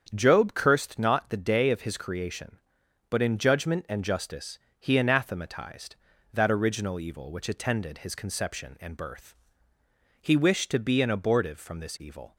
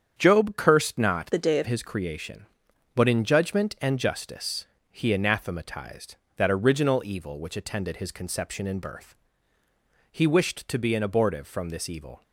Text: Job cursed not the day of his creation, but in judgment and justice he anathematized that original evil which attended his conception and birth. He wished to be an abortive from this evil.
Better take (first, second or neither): first